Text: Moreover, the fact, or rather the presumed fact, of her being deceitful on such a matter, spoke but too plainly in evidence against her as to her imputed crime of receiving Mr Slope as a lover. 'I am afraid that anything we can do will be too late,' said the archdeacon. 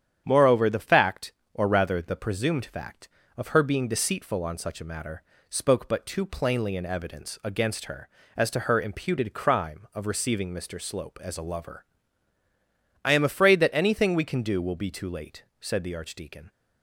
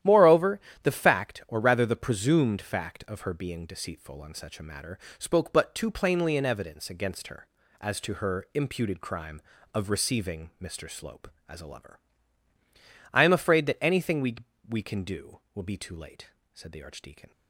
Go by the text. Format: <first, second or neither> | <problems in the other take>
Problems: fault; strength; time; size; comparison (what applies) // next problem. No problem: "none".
first | starts louder than the rest; strong; until 1.2 s; 11.5 dB; strong in the first // says "we" twice; at 14.6 s